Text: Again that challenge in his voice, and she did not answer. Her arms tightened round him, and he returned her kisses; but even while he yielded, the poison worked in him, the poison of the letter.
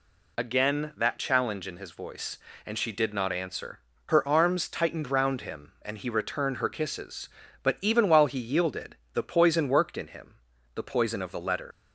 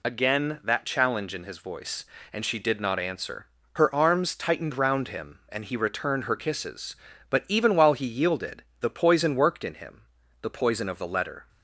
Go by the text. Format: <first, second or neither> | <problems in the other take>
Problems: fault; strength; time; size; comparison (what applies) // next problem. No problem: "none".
second | leaves "letter" unfinished; at 11.7 s; 105 ms